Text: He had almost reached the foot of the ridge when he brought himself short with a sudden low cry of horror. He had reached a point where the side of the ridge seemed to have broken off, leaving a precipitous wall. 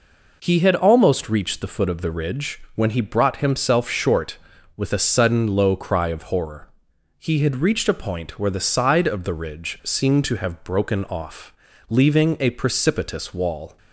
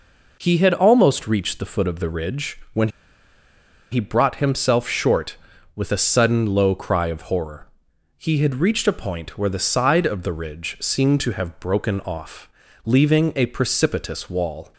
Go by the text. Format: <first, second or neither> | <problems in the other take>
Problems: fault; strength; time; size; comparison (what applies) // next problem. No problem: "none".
first | pauses between "when" and "he"; at 2.8 s; 1.0 s long